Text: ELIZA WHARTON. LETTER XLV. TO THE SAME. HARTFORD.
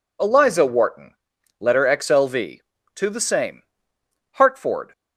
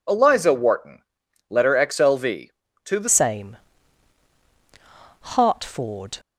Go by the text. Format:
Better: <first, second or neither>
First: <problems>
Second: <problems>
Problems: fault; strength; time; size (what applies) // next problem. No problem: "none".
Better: first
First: none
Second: changes voice at "SAME"; from 3.0 s on; 3.1 s long